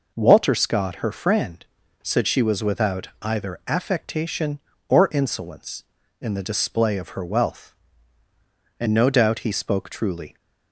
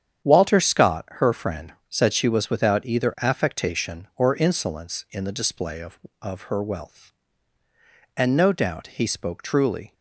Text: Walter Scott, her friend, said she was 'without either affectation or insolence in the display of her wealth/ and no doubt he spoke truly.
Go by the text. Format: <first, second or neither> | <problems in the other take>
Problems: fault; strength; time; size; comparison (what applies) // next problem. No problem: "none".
first | starts louder than the rest; strong; until 1.3 s; 8.5 dB // says "of" twice; at 6.1 s